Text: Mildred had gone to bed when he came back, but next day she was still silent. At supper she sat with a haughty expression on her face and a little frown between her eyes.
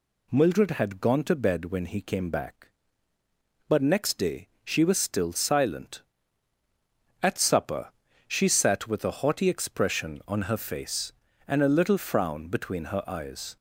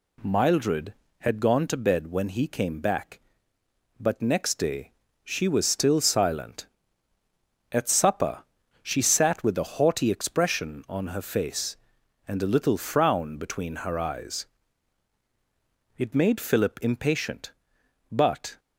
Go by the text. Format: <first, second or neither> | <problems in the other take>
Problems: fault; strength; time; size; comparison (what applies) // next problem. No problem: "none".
first | pauses between "day" and "she"; slight; at 4.9 s; 0.32 s long // pauses between "supper" and "she"; at 8.4 s; 0.40 s long; also in the first // goes on to say "It made Philip impatient but"; strong; from 15.9 s on; 2.6 s long